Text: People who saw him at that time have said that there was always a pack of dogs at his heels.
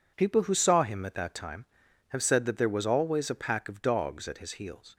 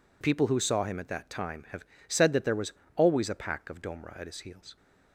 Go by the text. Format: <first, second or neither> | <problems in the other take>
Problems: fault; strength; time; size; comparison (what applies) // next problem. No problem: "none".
first | pauses between "have" and "said"; slight; at 1.8 s; 0.24 s long // pauses between "was" and "always"; slight; at 2.7 s; 0.24 s long // says "domra" for "dogs"; at 3.8 s